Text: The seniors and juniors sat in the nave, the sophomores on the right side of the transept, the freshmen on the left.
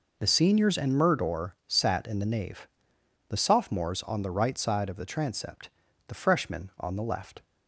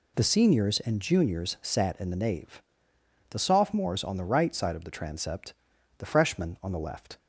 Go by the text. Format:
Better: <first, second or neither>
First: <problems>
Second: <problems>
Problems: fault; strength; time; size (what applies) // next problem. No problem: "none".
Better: second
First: says "murdor" for "juniors"; at 0.9 s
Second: none